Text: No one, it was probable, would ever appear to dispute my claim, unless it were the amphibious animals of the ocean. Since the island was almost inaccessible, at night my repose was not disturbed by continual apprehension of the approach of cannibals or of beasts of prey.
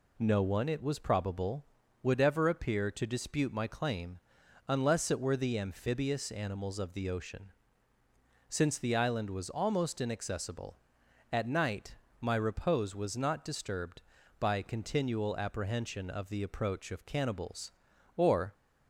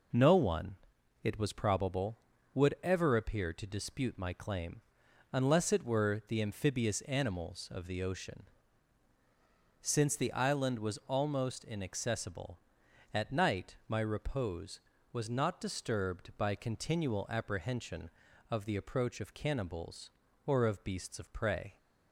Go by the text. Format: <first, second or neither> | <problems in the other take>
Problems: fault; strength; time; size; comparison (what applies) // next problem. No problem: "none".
second | pauses between "night" and "my"; slight; at 11.9 s; 0.26 s long // stops before "of beasts of prey"; at 18.5 s